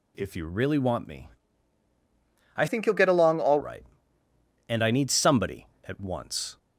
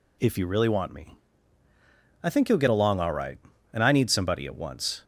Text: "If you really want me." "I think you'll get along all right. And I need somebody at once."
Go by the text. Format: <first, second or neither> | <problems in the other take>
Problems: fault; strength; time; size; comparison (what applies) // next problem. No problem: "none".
second | changes voice from "think" to "all"; from 2.6 to 3.6 s; 1.0 s long